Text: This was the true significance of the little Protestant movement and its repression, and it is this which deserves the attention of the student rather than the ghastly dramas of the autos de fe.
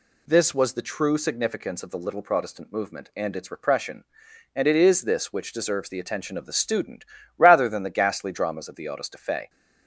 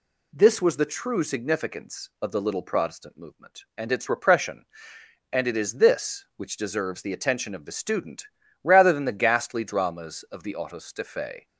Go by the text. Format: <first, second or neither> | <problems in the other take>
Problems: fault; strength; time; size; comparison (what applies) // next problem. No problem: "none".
neither | pauses between "student" and "rather"; the same in both